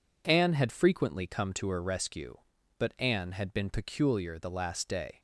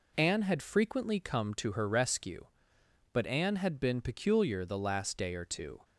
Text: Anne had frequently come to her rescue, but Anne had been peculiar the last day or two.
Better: second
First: stops before "or two"; at 5.1 s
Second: none

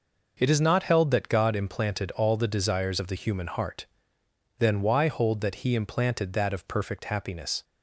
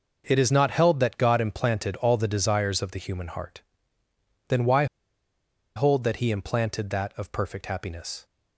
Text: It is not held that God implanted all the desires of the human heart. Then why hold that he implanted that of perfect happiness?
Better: first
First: none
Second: pauses between "why" and "hold"; noticeable; at 4.8 s; 0.90 s long

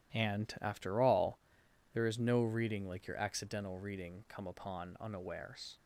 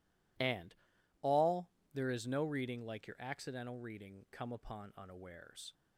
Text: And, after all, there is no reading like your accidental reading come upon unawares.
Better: first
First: none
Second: skips "after"; at 0.9 s

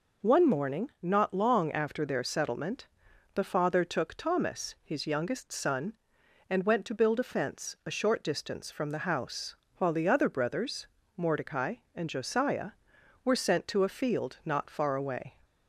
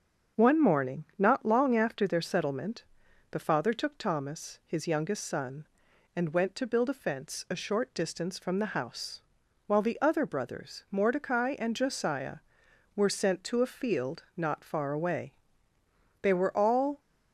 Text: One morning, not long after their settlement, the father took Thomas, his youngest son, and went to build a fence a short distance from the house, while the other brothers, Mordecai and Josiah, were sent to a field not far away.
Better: first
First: none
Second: starts louder than the rest; strong; until 1.4 s; 7 dB // goes on to say "They were all"; noticeable; from 16.1 s on; 0.80 s long

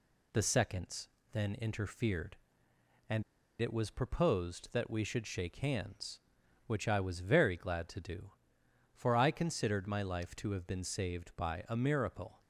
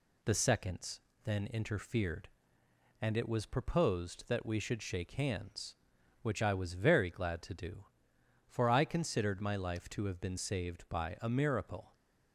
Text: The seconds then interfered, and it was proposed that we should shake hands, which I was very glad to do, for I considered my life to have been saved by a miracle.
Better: second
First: pauses between "seconds" and "then"; slight; at 1.0 s; 0.24 s long // pauses between "and" and "it"; at 3.2 s; 0.39 s long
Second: pauses between "seconds" and "then"; slight; at 0.9 s; 0.24 s long

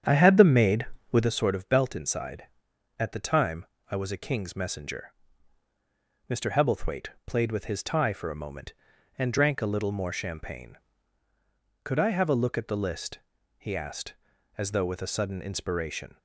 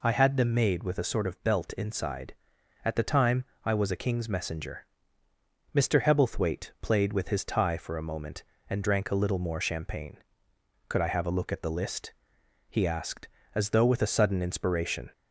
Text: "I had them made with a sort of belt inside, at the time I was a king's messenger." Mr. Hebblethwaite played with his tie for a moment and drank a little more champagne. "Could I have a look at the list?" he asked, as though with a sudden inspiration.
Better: second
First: starts louder than the rest; strong; until 1.3 s; 8.5 dB // pauses between "time" and "I"; slight; at 3.6 s; 0.24 s long // pauses between "Hebblethwaite" and "played"; slight; at 7.0 s; 0.16 s long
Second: pauses between "time" and "I"; slight; at 3.4 s; 0.20 s long

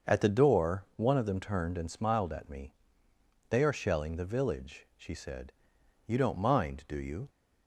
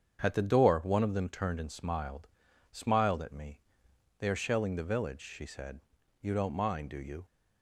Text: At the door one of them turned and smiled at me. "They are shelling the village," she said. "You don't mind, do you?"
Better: first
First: starts louder than the rest; until 1.1 s; 6.5 dB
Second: starts louder than the rest; strong; until 1.2 s; 7.5 dB // says "smiled" twice; at 2.7 s

